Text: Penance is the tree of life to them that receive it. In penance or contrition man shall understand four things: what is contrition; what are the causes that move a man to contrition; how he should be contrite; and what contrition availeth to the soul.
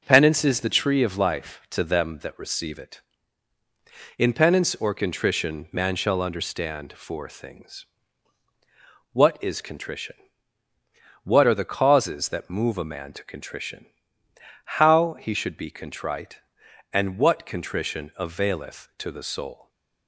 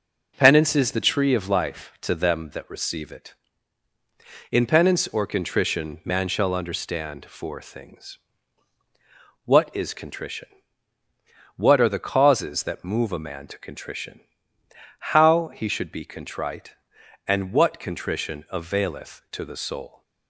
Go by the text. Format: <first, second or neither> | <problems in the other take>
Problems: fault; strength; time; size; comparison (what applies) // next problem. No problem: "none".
neither | none